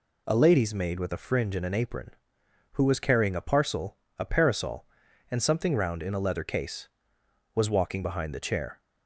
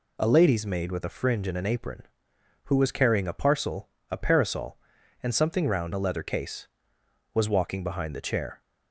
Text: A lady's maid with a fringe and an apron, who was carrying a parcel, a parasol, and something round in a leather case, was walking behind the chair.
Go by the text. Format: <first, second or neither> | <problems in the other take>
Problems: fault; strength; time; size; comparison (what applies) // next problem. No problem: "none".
first | skips "in"; at 5.9 s